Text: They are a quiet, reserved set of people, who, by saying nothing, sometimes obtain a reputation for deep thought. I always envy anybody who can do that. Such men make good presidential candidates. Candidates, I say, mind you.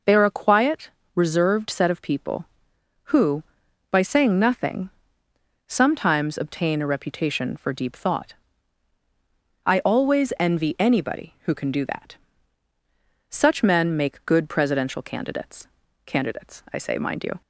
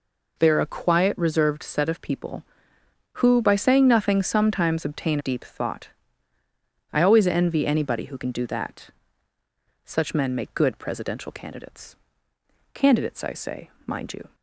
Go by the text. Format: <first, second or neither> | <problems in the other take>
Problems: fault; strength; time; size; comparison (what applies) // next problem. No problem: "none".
first | skips "a reputation for"; at 5.1 s